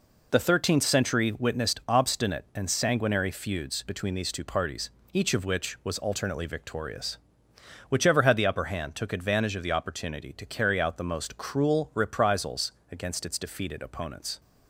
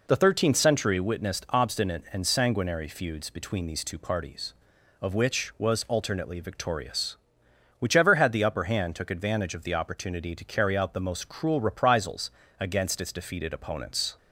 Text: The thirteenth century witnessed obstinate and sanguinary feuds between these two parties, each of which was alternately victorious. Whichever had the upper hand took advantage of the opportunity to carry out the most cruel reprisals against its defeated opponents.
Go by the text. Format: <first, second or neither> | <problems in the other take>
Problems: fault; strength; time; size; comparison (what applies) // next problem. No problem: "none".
first | skips "each"; at 4.7 s // pauses between "reprisals" and "against"; slight; at 12.3 s; 0.26 s long; slight in the first